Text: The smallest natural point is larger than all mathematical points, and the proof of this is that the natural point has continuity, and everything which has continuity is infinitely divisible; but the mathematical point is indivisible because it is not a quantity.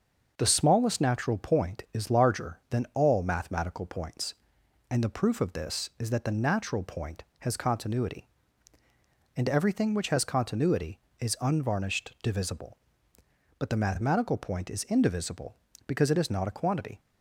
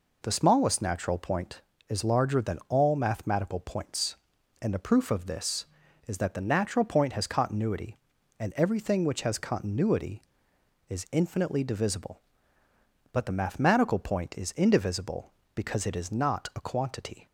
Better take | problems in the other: second | starts louder than the rest; until 1.3 s; 6.5 dB // says "unvarnished" for "infinitely"; at 11.3 s

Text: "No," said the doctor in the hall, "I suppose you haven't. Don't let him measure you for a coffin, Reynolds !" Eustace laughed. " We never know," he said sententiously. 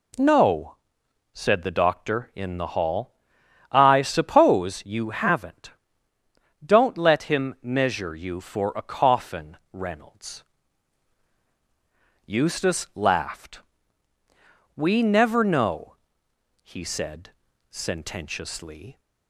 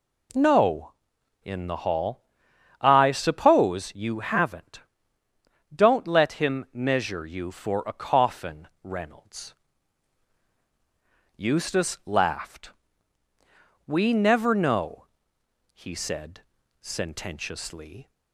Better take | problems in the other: first | skips "said the doctor"; at 1.1 s // pauses between "said" and "sententiously"; at 16.4 s; 0.40 s long; also in the first

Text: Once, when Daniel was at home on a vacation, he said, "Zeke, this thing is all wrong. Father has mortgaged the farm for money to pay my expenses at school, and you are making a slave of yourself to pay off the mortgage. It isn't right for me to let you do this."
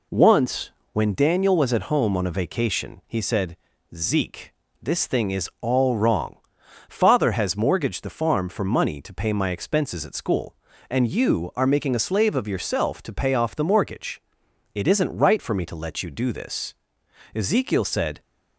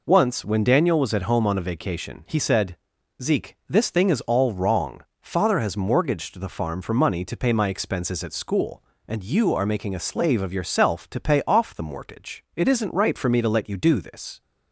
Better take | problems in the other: second | goes on to say "Ezekiel said"; noticeable; from 17.3 s on; 0.86 s long

